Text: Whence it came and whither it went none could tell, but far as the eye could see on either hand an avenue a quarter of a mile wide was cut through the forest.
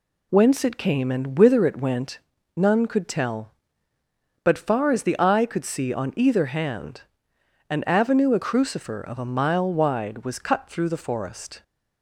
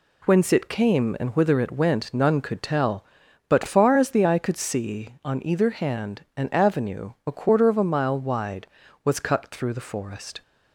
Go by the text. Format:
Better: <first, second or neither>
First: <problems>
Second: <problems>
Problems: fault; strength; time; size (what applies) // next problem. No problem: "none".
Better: second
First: pauses between "went" and "none"; slight; at 2.2 s; 0.36 s long // pauses between "hand" and "an"; noticeable; at 7.0 s; 0.68 s long // says "crucifer" for "quarter"; at 8.4 s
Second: none